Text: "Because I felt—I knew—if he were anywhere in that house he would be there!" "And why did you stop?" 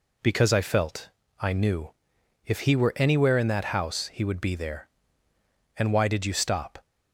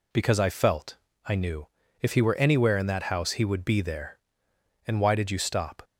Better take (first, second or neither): neither